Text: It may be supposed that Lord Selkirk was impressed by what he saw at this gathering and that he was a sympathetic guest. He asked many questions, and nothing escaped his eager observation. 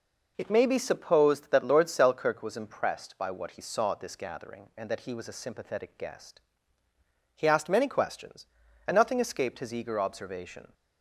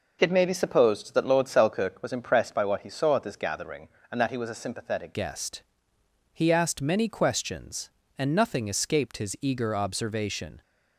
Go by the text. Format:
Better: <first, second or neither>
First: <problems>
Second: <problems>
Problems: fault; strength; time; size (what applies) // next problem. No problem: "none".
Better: first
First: none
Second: changes voice at "guest"; from 5.1 s on; 5.5 s long